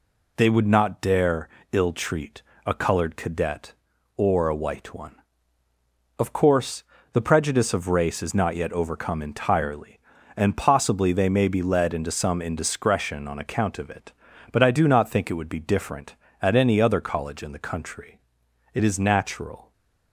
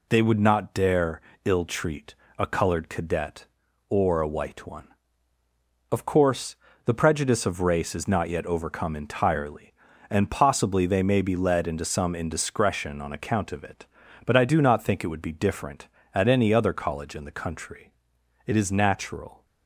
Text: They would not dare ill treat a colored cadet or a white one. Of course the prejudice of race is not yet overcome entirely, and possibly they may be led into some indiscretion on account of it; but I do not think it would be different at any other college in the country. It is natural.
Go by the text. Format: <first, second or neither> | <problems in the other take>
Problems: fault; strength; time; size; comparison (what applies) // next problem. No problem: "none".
neither | pauses between "dare" and "ill"; slight; the same in both // pauses between "treat" and "a"; slight; the same in both // pauses between "course" and "the"; slight; the same in both